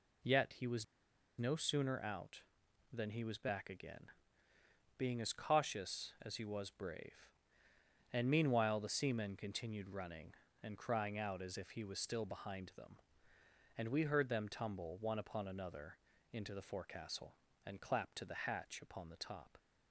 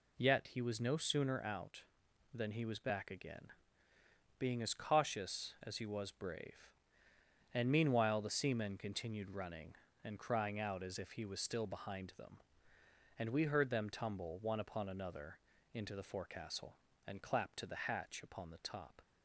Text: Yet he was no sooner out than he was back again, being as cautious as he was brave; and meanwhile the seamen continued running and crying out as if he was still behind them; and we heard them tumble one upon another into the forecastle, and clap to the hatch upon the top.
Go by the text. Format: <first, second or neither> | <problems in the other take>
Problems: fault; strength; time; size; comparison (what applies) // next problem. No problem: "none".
second | pauses between "was" and "no"; noticeable; at 0.8 s; 0.53 s long // pauses between "another" and "into"; slight; at 15.9 s; 0.36 s long; slight in the second